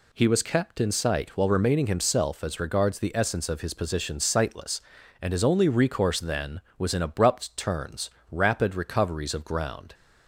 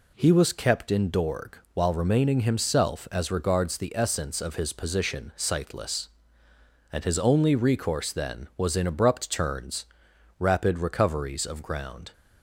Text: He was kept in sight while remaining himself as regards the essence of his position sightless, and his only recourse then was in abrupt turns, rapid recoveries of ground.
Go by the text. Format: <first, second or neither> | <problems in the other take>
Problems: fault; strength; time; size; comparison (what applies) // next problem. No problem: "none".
first | says "dorg" for "sight"; at 1.1 s